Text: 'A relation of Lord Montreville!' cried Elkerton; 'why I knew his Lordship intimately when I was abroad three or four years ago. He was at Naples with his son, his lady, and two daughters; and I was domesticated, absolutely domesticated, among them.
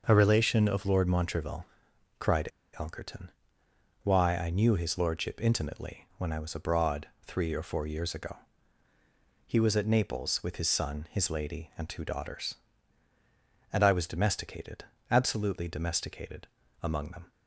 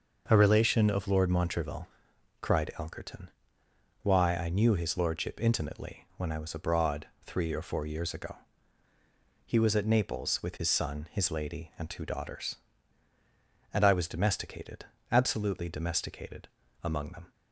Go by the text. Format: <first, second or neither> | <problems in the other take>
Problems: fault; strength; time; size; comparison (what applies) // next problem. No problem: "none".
second | pauses between "cried" and "Elkerton"; slight; at 2.5 s; 0.26 s long // pauses between "abroad" and "three"; slight; at 7.0 s; 0.16 s long; slight in the second